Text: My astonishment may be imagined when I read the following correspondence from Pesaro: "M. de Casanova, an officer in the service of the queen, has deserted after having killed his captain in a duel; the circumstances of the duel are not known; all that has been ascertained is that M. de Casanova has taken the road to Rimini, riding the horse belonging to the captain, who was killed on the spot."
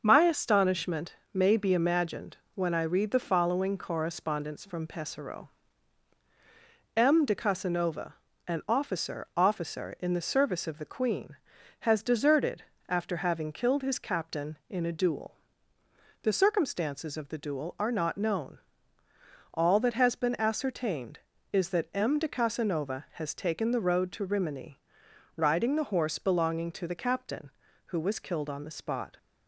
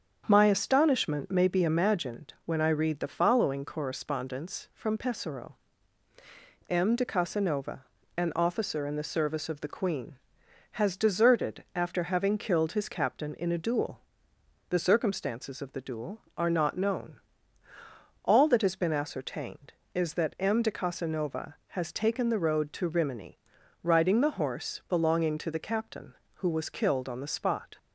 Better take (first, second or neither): second